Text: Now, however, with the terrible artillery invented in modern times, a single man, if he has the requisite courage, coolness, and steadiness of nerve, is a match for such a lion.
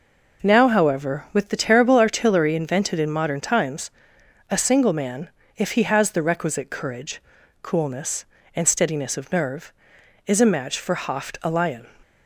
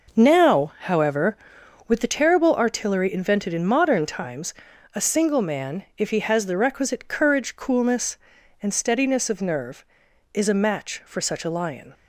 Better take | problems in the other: second | says "hoft" for "such"; at 10.9 s

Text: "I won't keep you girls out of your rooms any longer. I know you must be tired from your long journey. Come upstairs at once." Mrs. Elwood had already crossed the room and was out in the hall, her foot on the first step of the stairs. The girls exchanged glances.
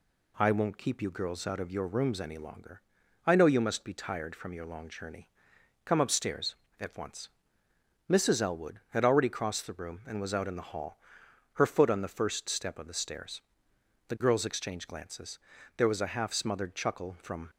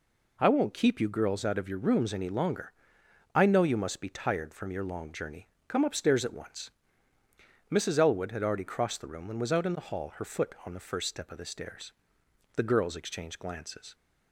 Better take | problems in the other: second | goes on to say "There was a half smothered chuckle from"; strong; from 15.7 s on; 1.7 s long

